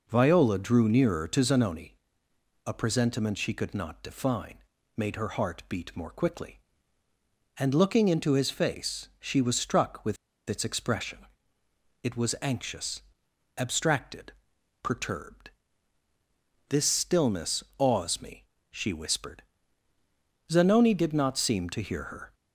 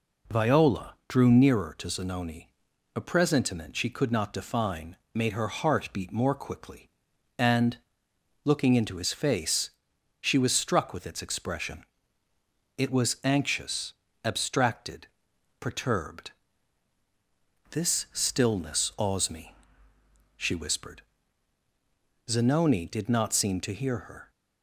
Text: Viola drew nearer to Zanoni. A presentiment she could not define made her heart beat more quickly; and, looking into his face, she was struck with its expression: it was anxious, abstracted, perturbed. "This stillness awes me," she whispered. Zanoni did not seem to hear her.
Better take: second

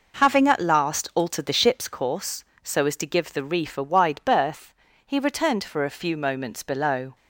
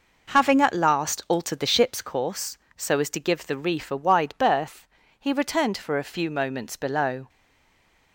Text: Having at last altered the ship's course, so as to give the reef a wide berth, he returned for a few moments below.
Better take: first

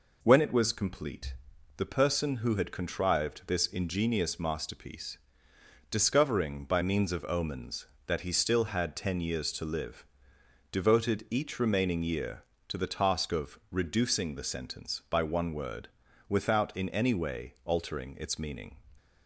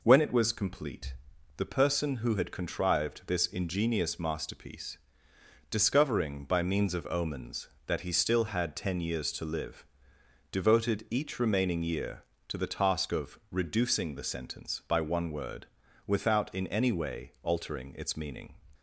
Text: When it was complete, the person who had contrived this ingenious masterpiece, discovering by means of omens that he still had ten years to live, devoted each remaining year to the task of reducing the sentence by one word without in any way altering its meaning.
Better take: neither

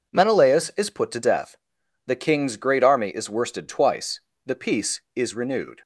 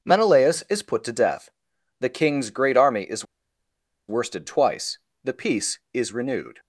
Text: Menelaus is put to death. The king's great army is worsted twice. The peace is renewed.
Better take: first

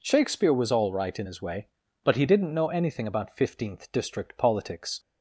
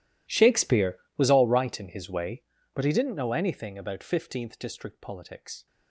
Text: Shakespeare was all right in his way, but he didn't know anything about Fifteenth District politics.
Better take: first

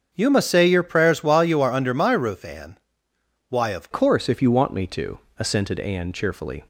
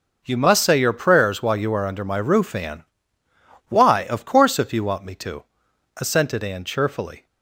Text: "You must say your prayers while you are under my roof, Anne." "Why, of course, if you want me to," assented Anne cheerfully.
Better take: second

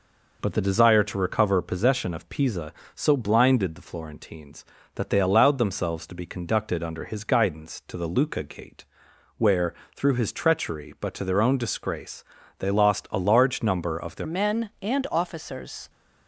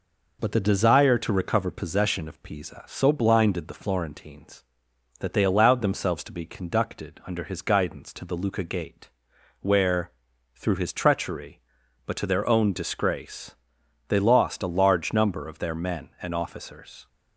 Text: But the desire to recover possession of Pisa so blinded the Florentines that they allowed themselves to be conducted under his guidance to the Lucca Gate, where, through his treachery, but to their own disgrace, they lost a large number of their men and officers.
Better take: second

